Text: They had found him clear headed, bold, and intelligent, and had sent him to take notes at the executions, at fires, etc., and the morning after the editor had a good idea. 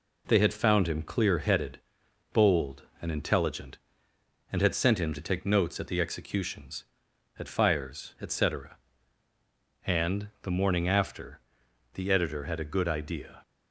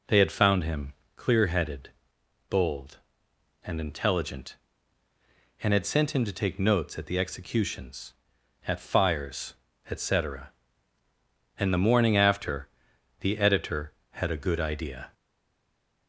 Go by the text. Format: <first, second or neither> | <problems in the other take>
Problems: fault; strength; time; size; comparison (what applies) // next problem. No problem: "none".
first | pauses between "him" and "clear"; slight; at 0.9 s; 0.22 s long // pauses between "after" and "the"; noticeable; at 12.6 s; 0.54 s long; noticeable in the first // stays silent after the last word; slight; from 15.1 s on; 0.9 s long